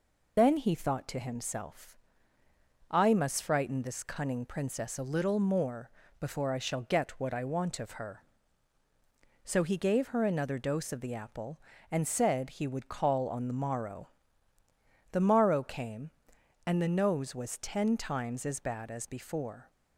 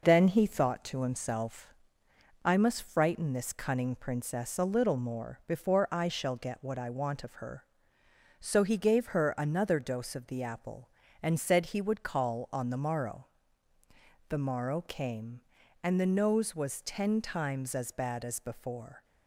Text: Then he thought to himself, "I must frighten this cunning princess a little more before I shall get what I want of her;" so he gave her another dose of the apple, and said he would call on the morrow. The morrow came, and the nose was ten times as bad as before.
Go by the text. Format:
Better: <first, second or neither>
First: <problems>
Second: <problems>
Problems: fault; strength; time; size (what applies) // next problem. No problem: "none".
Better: second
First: loses the start of "Then"; at 0.3 s; 90 ms // pauses between "more" and "before"; slight; at 5.9 s; 0.30 s long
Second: none